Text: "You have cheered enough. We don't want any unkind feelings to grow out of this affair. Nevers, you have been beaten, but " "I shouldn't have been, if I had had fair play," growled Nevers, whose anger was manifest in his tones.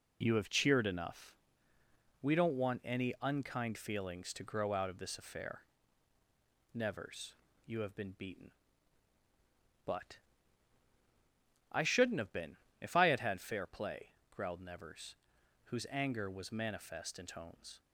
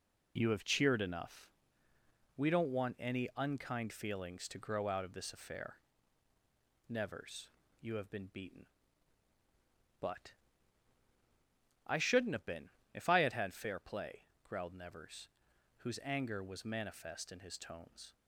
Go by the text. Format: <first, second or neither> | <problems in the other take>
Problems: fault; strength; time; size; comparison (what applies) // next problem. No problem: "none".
second | skips "his"; at 17.2 s